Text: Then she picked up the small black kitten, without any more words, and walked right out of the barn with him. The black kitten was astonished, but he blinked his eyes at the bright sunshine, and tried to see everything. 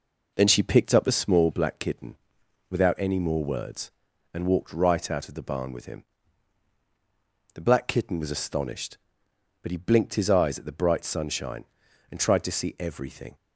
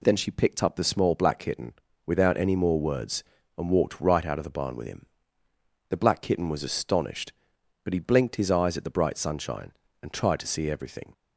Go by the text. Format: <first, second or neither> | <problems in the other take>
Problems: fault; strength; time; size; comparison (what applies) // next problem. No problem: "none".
second | starts louder than the rest; noticeable; until 1.5 s; 4.5 dB